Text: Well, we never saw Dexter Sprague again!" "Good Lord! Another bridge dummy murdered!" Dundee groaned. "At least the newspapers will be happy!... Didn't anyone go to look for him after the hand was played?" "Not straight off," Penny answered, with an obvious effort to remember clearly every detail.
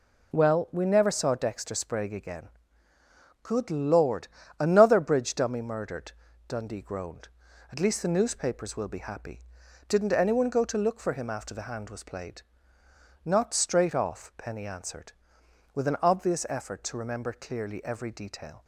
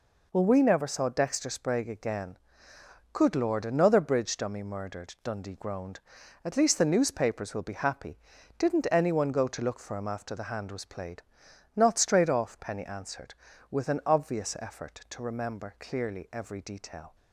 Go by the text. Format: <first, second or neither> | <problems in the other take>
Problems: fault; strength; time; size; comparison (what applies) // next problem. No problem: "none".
neither | none